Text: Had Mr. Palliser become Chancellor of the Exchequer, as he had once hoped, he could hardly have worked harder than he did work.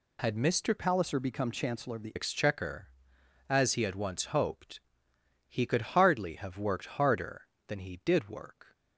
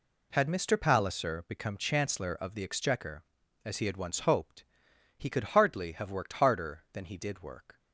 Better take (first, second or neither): second